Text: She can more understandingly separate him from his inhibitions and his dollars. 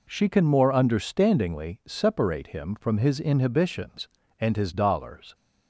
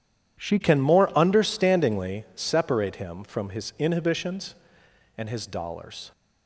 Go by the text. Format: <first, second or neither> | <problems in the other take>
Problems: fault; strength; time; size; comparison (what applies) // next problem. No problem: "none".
first | changes voice at "can"; from 0.6 s on; 5.5 s long